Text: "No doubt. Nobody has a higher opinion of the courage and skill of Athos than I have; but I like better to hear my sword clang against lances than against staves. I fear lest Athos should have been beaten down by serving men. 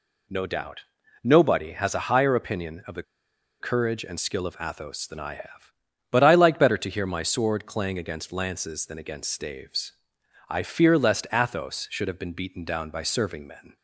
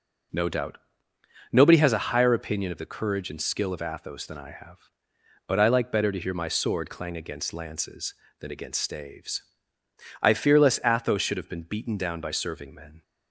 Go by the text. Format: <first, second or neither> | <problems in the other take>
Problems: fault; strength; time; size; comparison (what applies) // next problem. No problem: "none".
second | pauses between "the" and "courage"; noticeable; at 3.0 s; 0.57 s long